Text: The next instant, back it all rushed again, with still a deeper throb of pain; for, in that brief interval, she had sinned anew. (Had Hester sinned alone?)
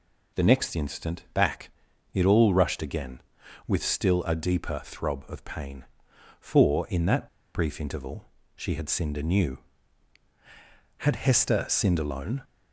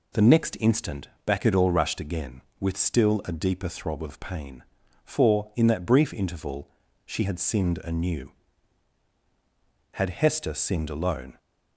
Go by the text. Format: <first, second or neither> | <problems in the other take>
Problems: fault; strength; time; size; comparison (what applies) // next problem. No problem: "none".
second | pauses between "back" and "it"; at 1.6 s; 0.44 s long // pauses between "that" and "brief"; slight; at 7.2 s; 0.27 s long